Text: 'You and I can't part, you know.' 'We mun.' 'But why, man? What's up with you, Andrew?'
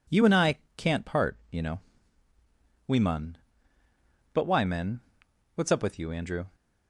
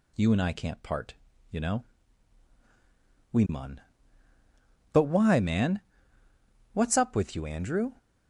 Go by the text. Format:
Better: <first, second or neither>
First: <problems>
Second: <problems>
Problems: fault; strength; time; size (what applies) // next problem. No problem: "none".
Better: second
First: pauses between "I" and "can't"; slight; at 0.5 s; 0.22 s long // says "men" for "man"; at 4.6 s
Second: none